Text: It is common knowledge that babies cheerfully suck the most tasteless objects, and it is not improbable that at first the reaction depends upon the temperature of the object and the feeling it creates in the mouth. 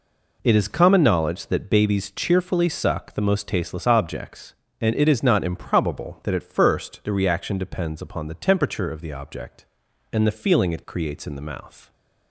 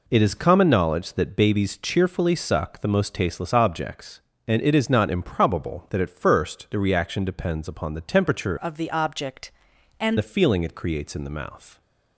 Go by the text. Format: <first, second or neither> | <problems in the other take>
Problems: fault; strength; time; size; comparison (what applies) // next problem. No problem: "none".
first | changes voice from "of" to "and"; from 8.6 to 10.1 s; 1.5 s long